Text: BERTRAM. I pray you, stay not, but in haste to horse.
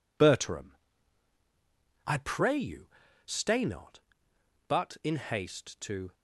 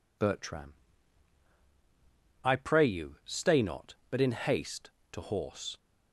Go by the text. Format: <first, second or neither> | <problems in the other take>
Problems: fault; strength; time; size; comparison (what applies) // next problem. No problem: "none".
second | stops before "horse"; at 6.1 s